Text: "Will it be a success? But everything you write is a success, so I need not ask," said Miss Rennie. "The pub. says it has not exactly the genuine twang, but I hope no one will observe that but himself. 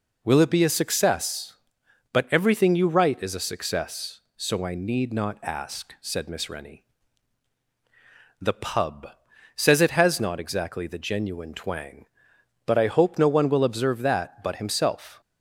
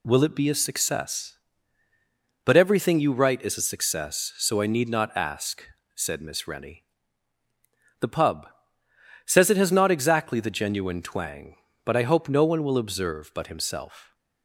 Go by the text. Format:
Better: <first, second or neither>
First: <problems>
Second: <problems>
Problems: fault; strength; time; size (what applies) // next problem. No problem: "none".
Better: first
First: none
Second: skips "that"; at 13.3 s